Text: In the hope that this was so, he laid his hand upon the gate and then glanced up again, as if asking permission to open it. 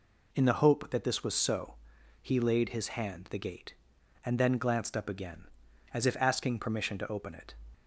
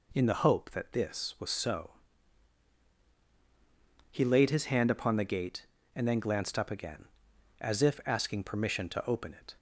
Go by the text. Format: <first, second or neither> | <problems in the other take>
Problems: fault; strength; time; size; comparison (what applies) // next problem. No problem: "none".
second | skips "upon"; at 3.2 s